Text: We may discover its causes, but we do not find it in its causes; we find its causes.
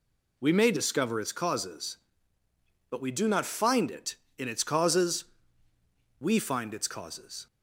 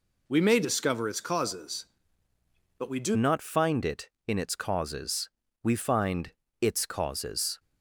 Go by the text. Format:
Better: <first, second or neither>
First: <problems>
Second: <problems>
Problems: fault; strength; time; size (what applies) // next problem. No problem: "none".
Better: first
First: none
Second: changes voice at "not"; from 3.1 s on; 4.4 s long // pauses between "find" and "its"; slight; at 6.3 s; 0.26 s long